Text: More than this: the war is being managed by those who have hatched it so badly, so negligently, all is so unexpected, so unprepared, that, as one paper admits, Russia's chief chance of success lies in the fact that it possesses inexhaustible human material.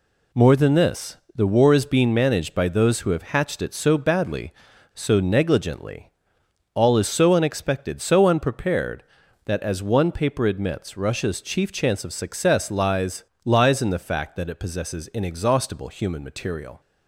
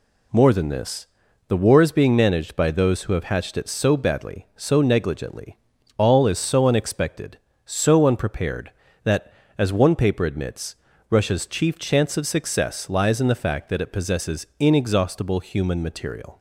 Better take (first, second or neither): second